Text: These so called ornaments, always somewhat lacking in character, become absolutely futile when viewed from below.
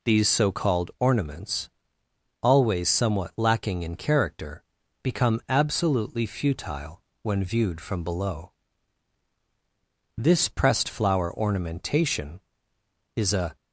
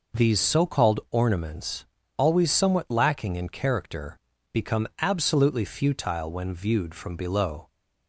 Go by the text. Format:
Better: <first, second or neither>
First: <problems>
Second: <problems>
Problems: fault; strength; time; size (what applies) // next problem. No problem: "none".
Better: second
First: pauses between "futile" and "when"; slight; at 7.0 s; 0.20 s long // goes on to say "This pressed flower ornamentation is a"; strong; from 10.1 s on; 3.3 s long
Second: none